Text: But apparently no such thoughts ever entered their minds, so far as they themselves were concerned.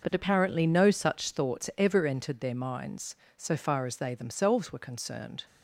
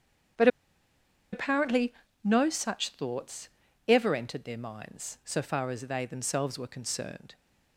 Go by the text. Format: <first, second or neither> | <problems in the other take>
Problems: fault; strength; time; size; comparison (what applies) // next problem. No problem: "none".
first | starts louder than the rest; strong; until 2.5 s; 8 dB // pauses between "But" and "apparently"; noticeable; at 0.4 s; 0.85 s long // pauses between "apparently" and "no"; slight; at 1.9 s; 0.30 s long // pauses between "thoughts" and "ever"; at 3.4 s; 0.40 s long